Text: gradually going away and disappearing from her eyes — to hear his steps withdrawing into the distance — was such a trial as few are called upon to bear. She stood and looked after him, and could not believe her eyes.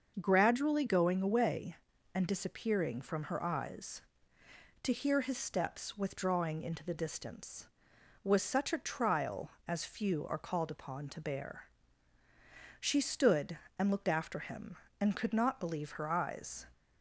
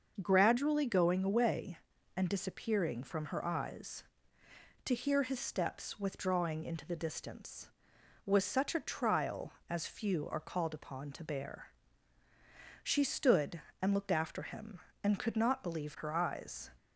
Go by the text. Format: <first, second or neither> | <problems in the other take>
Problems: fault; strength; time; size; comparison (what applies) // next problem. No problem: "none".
neither | starts louder than the rest; the same in both